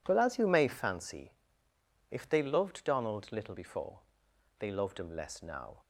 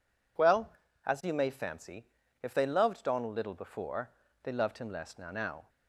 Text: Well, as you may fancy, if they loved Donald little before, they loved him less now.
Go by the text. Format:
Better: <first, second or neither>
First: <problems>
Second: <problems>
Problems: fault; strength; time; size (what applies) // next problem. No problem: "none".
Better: first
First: none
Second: says "now" twice; at 5.3 s